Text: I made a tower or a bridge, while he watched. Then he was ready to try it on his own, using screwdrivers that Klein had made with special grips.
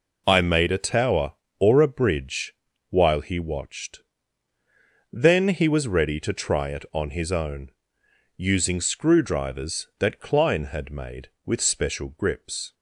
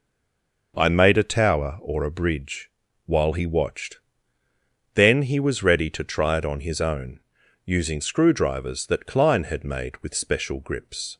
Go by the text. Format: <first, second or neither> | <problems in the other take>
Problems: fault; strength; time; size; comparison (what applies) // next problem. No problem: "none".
first | stays silent before the first word; slight; until 0.7 s; 0.7 s long